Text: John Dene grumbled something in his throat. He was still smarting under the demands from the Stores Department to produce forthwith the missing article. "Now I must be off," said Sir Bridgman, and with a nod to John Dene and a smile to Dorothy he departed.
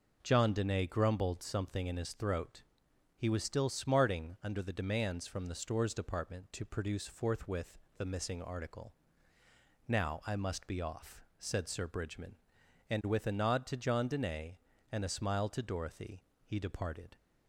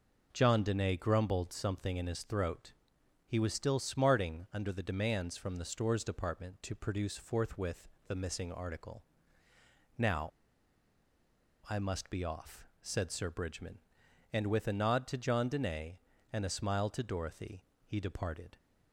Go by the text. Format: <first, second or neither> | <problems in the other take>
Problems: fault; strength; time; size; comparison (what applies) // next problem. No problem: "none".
first | pauses between "forthwith" and "the"; slight; at 7.8 s; 0.18 s long; slight in the first // pauses between "Now" and "I"; strong; at 10.3 s; 1.3 s long // pauses between "Dorothy" and "he"; slight; at 17.6 s; 0.22 s long; slight in the first